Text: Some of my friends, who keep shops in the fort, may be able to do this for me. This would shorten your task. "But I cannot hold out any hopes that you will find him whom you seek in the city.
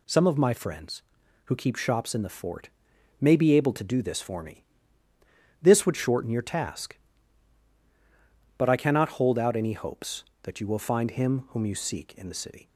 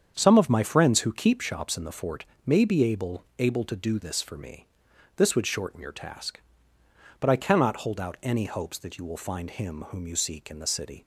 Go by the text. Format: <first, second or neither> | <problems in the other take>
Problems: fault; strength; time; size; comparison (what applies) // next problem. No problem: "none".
first | starts louder than the rest; strong; until 1.1 s; 7.5 dB // says "able" twice; at 3.3 s